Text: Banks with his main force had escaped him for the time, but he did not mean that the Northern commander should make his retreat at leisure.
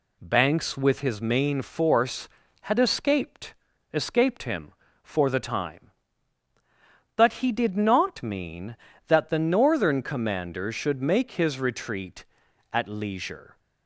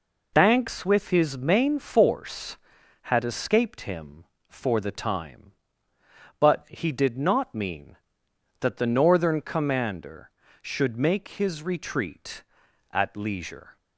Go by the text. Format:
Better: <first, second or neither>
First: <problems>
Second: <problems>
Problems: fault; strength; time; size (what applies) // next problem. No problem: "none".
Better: second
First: says "escaped" twice; at 3.9 s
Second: none